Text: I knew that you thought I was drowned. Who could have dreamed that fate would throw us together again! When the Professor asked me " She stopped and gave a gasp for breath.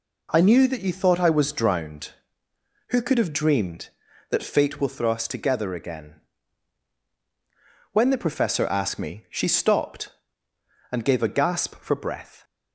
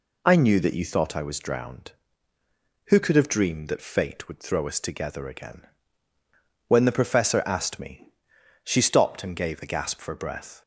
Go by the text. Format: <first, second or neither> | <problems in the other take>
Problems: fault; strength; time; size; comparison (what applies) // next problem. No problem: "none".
second | says "will" for "would"; at 4.7 s